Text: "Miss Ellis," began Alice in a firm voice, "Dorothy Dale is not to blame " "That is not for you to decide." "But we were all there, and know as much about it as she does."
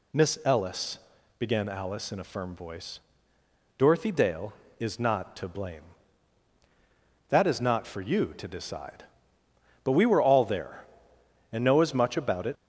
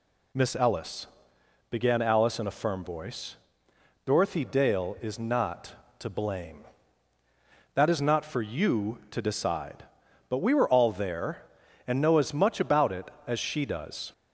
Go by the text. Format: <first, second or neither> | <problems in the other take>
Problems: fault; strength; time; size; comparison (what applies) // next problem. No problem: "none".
second | stops before "as she does"; at 12.5 s